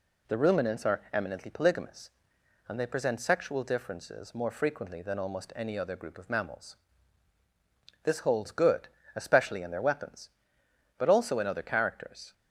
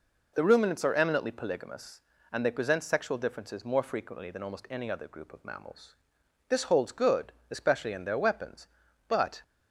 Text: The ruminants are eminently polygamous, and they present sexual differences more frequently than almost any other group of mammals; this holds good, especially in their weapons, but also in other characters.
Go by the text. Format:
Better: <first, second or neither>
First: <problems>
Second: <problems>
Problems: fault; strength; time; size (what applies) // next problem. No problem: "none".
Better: first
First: none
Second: stops before "also in other characters"; at 9.4 s